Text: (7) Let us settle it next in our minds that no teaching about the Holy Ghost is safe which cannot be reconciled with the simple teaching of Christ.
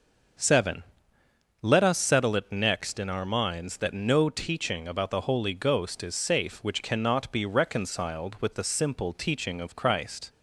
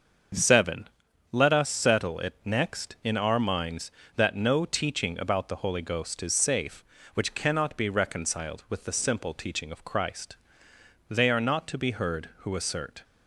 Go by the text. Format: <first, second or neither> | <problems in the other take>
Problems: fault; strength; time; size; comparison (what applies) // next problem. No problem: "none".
first | starts louder than the rest; until 1.7 s; 6.5 dB; also in the first // goes on to say "They are not to be heard who assert"; strong; from 11.0 s on; 1.9 s long